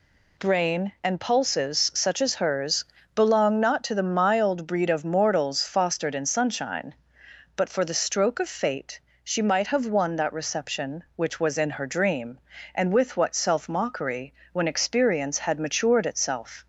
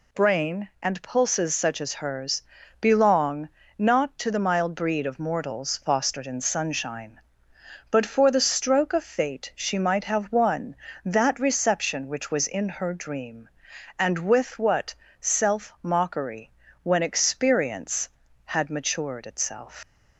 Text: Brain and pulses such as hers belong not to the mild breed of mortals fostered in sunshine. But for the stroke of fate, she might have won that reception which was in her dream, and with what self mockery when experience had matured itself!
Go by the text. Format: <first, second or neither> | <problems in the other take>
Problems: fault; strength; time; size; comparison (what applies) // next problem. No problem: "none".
first | pauses between "hers" and "belong"; at 2.4 s; 0.38 s long; slight in the first // pauses between "belong" and "not"; slight; at 3.4 s; 0.32 s long // pauses between "what" and "self"; slight; at 14.9 s; 0.28 s long // pauses between "mockery" and "when"; slight; at 16.5 s; 0.32 s long; slight in the first // leaves "itself" unfinished; at 19.8 s; 115 ms